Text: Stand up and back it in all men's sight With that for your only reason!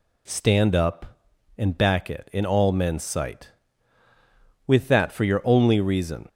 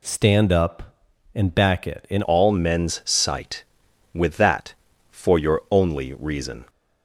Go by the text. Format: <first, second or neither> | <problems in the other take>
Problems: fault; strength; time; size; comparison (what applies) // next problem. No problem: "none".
first | changes voice at "all"; from 2.2 s on; 4.4 s long